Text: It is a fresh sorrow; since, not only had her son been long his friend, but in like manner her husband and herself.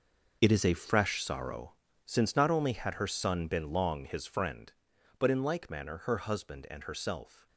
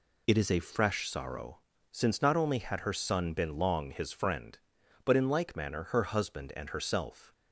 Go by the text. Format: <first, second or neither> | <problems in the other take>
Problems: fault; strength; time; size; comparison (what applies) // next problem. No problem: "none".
second | gets quieter; strong; throughout; 12.5 dB